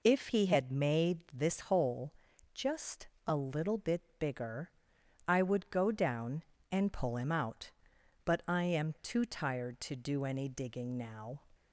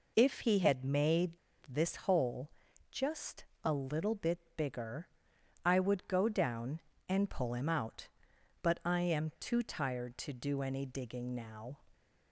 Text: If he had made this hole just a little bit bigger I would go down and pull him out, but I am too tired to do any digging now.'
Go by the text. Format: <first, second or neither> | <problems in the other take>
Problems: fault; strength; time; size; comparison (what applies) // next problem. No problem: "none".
first | pauses between "made" and "this"; slight; at 1.3 s; 0.34 s long // pauses between "hole" and "just"; at 2.5 s; 0.40 s long; also in the first // pauses between "just" and "a"; slight; at 3.4 s; 0.20 s long; slight in the first // pauses between "bit" and "bigger"; slight; at 4.3 s; 0.16 s long; slight in the first // pauses between "bigger" and "I"; noticeable; at 5.0 s; 0.58 s long; noticeable in the first